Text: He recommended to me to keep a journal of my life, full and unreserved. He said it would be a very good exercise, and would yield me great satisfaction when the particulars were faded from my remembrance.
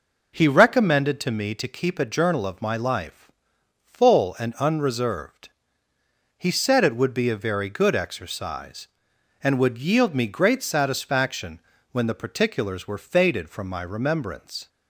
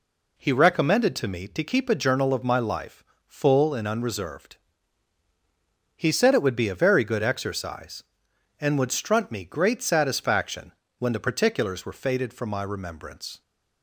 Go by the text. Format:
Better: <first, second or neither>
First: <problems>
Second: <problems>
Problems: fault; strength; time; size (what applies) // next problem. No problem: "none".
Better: first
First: pauses between "satisfaction" and "when"; slight; at 11.6 s; 0.32 s long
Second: says "strunt" for "yield"; at 8.8 s // pauses between "satisfaction" and "when"; slight; at 10.7 s; 0.28 s long